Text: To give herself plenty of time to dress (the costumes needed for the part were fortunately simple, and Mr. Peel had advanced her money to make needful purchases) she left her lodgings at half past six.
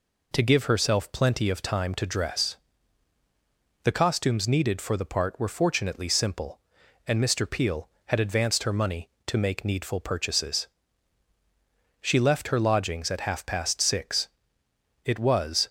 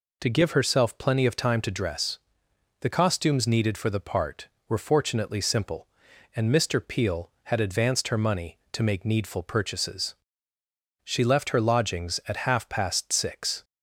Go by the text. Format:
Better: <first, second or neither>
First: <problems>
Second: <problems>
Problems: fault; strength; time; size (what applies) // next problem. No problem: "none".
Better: second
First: goes on to say "It was"; noticeable; from 15.0 s on; 0.64 s long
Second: none